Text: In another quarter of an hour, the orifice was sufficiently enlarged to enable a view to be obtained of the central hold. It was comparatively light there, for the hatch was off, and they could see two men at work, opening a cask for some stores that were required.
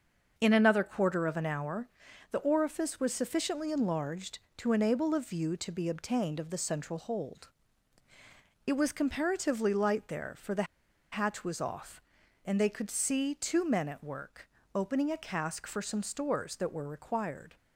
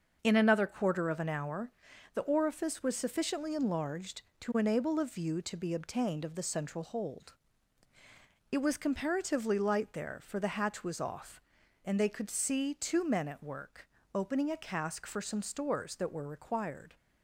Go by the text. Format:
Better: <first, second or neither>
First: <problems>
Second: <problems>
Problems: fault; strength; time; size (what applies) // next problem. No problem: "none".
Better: second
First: starts louder than the rest; until 1.3 s; 6.5 dB // pauses between "the" and "hatch"; noticeable; at 10.6 s; 0.47 s long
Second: starts louder than the rest; until 1.2 s; 6.5 dB